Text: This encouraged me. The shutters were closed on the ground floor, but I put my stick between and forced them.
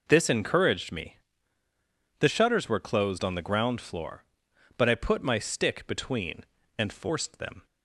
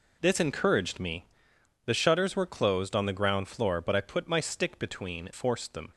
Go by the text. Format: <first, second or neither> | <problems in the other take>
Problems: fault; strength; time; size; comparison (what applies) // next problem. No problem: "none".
first | skips "and"; at 5.3 s